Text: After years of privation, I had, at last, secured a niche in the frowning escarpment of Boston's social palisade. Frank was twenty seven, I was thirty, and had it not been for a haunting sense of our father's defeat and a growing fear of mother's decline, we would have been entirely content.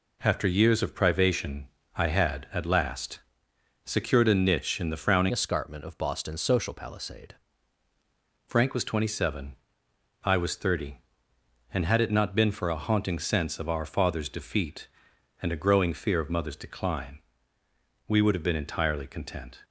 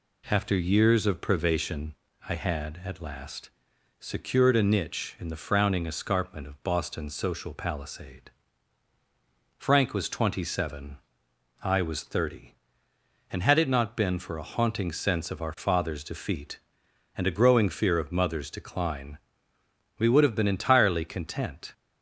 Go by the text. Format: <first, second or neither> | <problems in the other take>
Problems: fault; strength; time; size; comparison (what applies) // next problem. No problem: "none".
second | changes voice from "escarpment" to "palisade"; from 5.3 to 7.3 s; 2.0 s long